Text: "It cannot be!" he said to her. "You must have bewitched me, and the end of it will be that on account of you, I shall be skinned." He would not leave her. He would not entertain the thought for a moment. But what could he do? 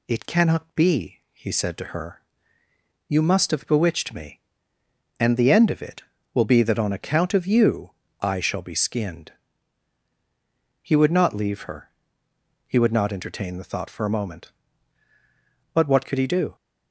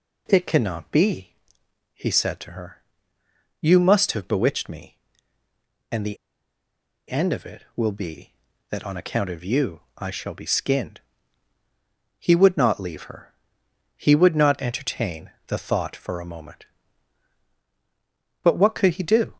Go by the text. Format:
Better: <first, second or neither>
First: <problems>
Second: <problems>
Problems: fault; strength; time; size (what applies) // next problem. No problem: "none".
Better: first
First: none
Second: pauses between "the" and "end"; noticeable; at 6.1 s; 0.91 s long // pauses between "entertain" and "the"; slight; at 15.3 s; 0.16 s long